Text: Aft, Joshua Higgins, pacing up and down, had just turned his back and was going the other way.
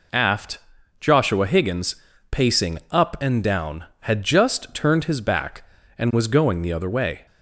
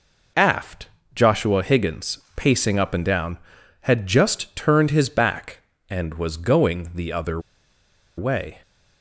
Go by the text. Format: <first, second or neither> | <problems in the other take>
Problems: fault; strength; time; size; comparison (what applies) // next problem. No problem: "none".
first | pauses between "other" and "way"; noticeable; at 7.3 s; 0.77 s long